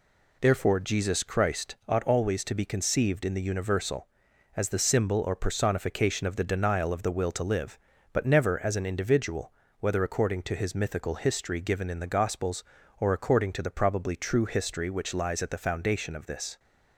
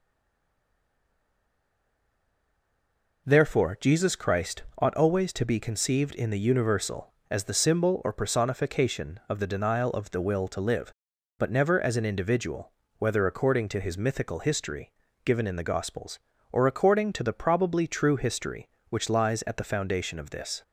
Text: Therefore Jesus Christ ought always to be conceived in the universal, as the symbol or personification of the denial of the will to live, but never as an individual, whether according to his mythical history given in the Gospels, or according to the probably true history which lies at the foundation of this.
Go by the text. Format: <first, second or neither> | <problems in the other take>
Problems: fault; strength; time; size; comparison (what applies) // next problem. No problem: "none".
first | stays silent before the first word; strong; until 3.2 s; 3.2 s long // pauses between "Christ" and "ought"; slight; at 4.6 s; 0.16 s long // pauses between "history" and "given"; slight; at 14.9 s; 0.34 s long